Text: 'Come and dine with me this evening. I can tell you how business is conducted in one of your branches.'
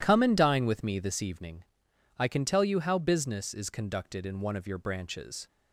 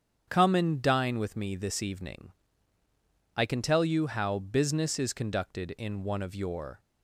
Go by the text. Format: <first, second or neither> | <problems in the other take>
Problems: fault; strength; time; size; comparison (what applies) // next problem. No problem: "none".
first | starts louder than the rest; strong; until 1.3 s; 8 dB // stops before "branches"; at 6.7 s